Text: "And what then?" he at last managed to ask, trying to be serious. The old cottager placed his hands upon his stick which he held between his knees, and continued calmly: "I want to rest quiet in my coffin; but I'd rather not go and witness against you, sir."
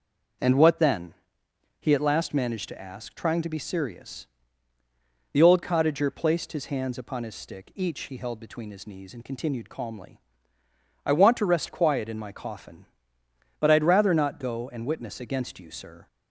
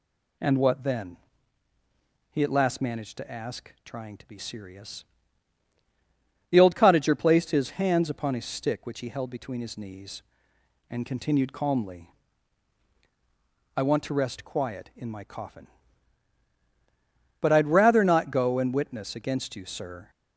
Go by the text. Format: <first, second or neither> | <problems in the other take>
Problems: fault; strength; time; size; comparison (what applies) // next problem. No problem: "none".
second | starts louder than the rest; until 2.0 s; 6 dB // says "each" for "which"; at 7.7 s